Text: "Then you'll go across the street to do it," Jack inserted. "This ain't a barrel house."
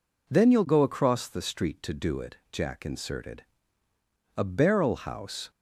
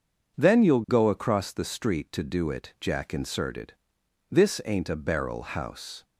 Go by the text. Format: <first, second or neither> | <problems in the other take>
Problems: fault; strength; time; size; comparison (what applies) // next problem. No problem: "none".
second | skips "This ain't"; at 3.9 s